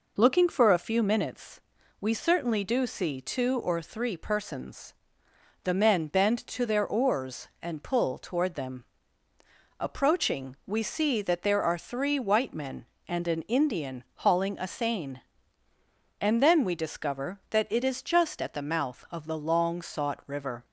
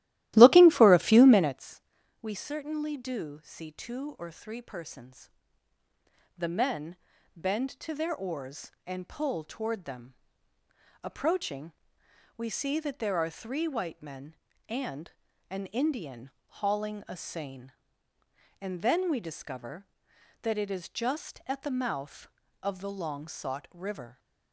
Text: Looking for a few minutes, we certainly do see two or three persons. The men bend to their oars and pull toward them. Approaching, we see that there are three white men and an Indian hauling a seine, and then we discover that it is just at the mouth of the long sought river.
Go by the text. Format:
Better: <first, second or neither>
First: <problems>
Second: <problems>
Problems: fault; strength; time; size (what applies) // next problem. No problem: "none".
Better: first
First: none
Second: starts louder than the rest; strong; until 1.6 s; 15 dB // pauses between "men" and "bend"; at 6.9 s; 0.40 s long // pauses between "and" and "an"; slight; at 15.1 s; 0.36 s long // pauses between "Indian" and "hauling"; slight; at 16.3 s; 0.28 s long